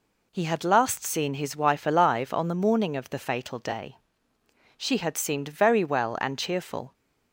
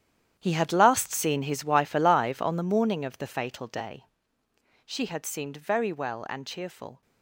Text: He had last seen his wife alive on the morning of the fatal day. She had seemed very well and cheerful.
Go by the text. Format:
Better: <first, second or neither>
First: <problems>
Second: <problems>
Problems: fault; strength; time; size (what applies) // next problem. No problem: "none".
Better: first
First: none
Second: gets quieter; strong; throughout; 14 dB